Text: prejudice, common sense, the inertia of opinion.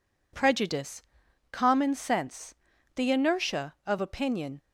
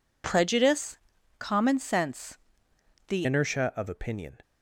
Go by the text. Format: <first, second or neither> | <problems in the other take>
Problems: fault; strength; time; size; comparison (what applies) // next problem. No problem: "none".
first | changes voice at "inertia"; from 3.2 s on; 1.1 s long